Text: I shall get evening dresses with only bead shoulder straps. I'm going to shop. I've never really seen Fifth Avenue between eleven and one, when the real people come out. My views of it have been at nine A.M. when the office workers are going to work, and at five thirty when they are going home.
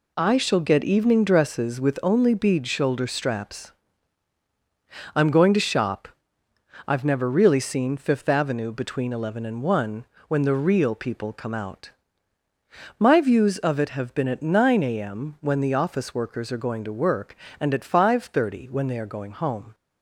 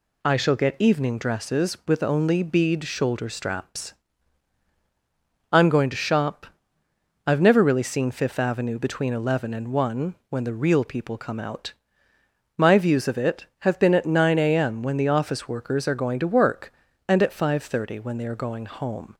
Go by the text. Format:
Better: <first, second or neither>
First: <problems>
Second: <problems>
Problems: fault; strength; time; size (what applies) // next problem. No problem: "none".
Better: neither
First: none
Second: none